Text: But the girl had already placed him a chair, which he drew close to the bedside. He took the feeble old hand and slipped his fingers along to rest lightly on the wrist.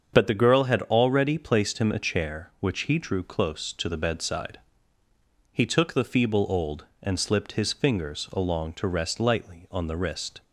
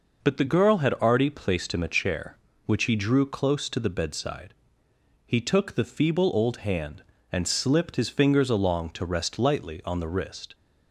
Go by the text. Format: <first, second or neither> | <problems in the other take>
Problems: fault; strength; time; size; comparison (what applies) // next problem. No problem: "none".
second | starts louder than the rest; until 1.1 s; 7 dB // skips "hand"; at 6.9 s